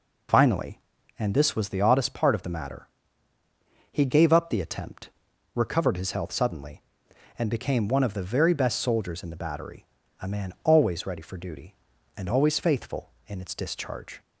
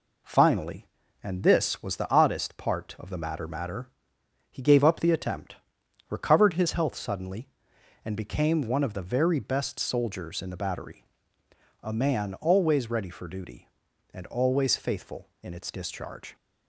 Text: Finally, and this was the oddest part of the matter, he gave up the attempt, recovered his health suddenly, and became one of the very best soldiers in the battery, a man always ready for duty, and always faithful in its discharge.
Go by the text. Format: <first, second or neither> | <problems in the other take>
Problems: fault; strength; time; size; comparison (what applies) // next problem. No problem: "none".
first | says "matter" twice; at 3.4 s